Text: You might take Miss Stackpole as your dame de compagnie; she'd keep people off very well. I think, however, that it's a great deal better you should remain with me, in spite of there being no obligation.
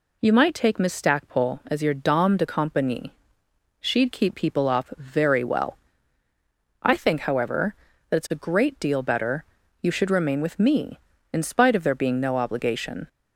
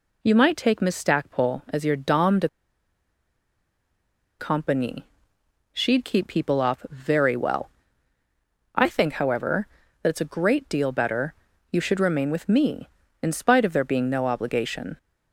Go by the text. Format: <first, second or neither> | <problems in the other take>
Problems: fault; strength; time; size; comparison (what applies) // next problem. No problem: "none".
first | pauses between "de" and "compagnie"; strong; at 2.4 s; 1.9 s long // pauses between "better" and "you"; at 11.3 s; 0.38 s long; also in the first